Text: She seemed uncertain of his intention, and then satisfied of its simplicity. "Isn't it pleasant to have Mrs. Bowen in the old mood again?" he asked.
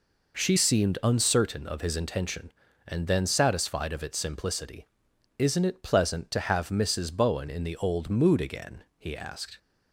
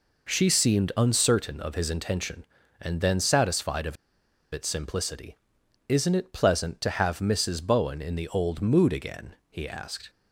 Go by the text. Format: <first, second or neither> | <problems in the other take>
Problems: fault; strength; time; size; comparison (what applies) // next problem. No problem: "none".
first | pauses between "of" and "its"; noticeable; at 3.9 s; 0.56 s long